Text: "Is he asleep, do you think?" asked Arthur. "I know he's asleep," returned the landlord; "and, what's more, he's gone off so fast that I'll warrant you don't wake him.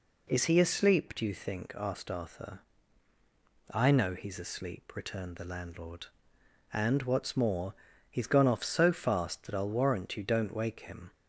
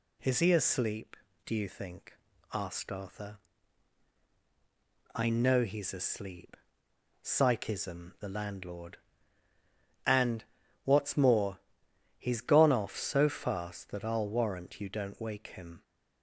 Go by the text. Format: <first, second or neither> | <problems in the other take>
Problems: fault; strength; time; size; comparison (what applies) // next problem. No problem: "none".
first | says "psychism" for "returned"; at 7.2 s